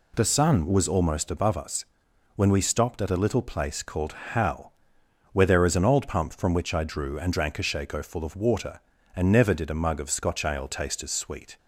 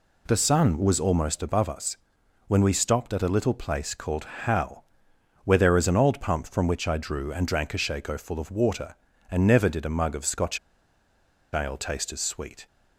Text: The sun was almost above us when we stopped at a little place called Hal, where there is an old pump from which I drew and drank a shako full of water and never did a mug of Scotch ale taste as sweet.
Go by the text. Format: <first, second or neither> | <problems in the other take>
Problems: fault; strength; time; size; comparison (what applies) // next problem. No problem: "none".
first | pauses between "us" and "when"; noticeable; at 1.9 s; 0.52 s long; noticeable in the first // pauses between "called" and "Hal"; slight; at 4.2 s; 0.18 s long; slight in the first // pauses between "Scotch" and "ale"; noticeable; at 10.5 s; 0.94 s long